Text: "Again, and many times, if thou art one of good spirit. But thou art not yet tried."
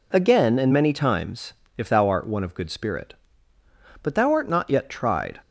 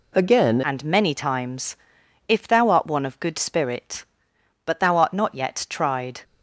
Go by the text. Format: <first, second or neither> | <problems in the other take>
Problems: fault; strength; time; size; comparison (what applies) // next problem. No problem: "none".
first | changes voice at "and"; from 0.6 s on; 5.6 s long